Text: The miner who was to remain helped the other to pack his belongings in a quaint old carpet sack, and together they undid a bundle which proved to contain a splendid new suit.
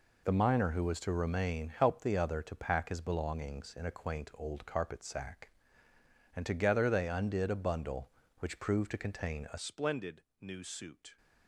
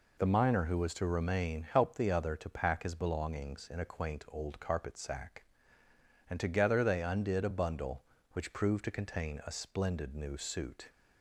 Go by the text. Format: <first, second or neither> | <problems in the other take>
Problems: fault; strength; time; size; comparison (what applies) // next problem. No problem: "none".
second | changes voice at "splendid"; from 9.5 s on; 1.6 s long // pauses between "splendid" and "new"; slight; at 10.2 s; 0.18 s long